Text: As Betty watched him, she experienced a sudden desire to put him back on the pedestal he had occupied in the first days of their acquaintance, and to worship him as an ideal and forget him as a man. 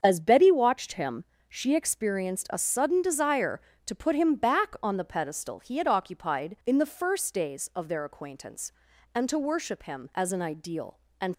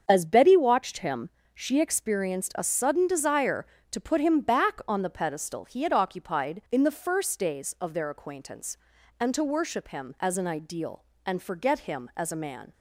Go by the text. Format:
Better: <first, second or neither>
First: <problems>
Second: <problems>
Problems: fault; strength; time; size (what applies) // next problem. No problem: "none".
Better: second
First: starts louder than the rest; until 1.0 s; 7 dB // stops before "forget him as a man"; at 11.3 s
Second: starts louder than the rest; until 1.0 s; 7 dB